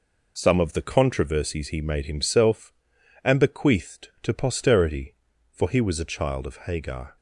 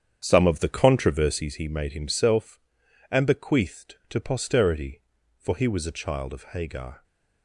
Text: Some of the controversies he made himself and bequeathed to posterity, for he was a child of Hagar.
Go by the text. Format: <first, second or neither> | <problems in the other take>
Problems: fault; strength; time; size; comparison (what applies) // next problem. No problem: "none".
first | starts louder than the rest; strong; until 1.5 s; 8.5 dB